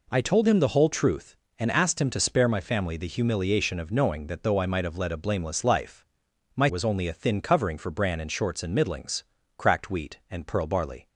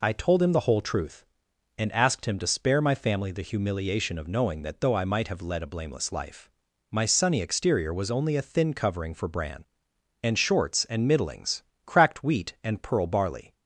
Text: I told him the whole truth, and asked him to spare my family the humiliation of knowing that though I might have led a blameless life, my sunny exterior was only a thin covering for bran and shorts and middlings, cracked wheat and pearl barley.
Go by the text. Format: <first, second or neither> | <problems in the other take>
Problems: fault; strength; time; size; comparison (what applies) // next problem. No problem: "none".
second | skips "sunny exterior"; at 6.6 s